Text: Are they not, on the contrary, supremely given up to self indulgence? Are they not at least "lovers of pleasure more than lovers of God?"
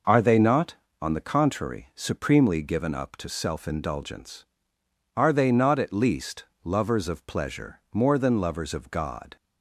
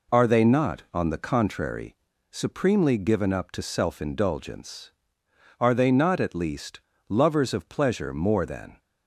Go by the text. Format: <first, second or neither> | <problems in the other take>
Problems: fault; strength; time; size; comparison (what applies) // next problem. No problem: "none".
first | pauses between "least" and "lovers"; slight; at 6.7 s; 0.28 s long; slight in the first // stops before "lovers of God"; at 8.7 s